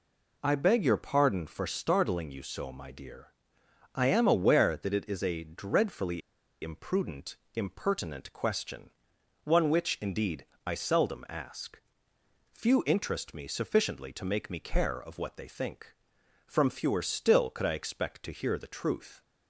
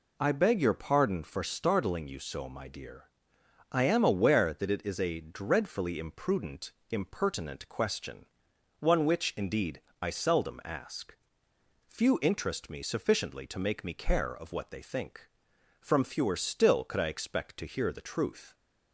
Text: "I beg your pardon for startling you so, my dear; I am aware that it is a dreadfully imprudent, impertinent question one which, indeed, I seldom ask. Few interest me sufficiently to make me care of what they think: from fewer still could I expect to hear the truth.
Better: second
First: pauses between "dreadfully" and "imprudent"; at 6.2 s; 0.42 s long // pauses between "question" and "one"; noticeable; at 8.8 s; 0.54 s long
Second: pauses between "question" and "one"; noticeable; at 8.2 s; 0.54 s long

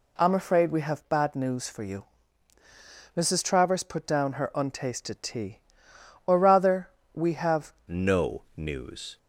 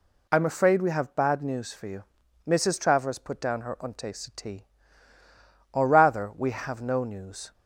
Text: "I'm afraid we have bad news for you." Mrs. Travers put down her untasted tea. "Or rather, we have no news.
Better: second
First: changes voice at "no"; from 7.8 s on; 1.3 s long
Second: none

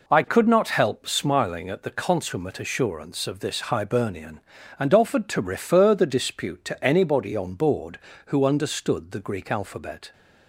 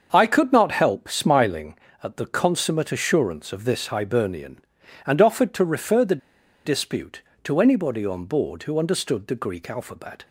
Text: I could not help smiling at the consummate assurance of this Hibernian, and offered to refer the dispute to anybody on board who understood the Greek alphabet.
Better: first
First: none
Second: starts louder than the rest; until 1.1 s; 6.5 dB // pauses between "the" and "dispute"; noticeable; at 6.1 s; 0.48 s long

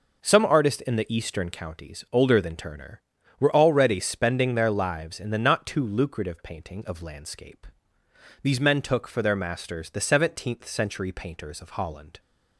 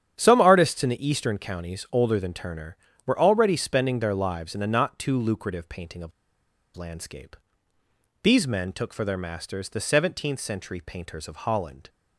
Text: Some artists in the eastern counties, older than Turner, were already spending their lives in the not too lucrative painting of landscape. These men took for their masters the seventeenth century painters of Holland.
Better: first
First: none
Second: starts louder than the rest; strong; until 1.1 s; 9 dB // pauses between "of" and "landscape"; noticeable; at 6.1 s; 0.65 s long

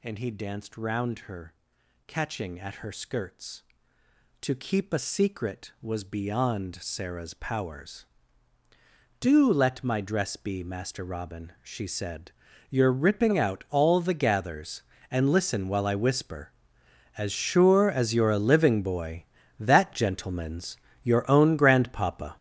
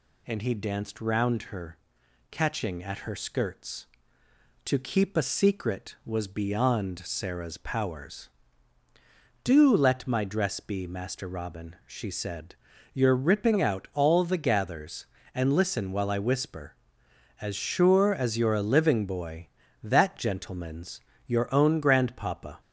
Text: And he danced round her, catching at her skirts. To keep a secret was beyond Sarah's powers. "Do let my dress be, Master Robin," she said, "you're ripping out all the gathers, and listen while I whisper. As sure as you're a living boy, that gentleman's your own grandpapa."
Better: second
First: gets louder; strong; throughout; 10 dB // pauses between "gentleman's" and "your"; slight; at 20.7 s; 0.26 s long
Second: pauses between "gentleman's" and "your"; slight; at 21.0 s; 0.26 s long

